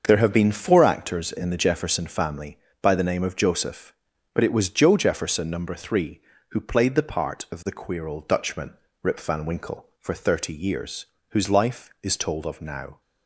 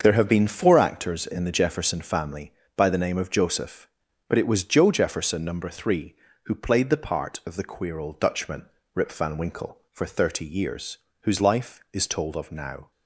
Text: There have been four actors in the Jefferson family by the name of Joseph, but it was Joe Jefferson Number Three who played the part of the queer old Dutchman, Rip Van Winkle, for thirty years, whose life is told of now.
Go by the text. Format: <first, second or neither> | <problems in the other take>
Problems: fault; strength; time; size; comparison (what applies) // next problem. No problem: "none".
neither | starts louder than the rest; the same in both